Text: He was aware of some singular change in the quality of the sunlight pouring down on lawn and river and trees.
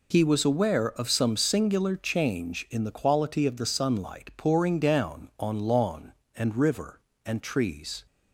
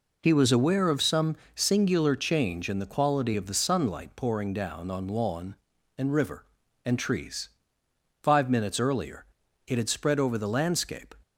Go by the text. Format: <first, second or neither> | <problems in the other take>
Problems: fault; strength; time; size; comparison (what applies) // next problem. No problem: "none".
first | pauses between "some" and "singular"; slight; at 1.3 s; 0.20 s long // goes on to say "Five minutes earlier it had spread over the landscape"; strong; from 8.2 s on; 2.9 s long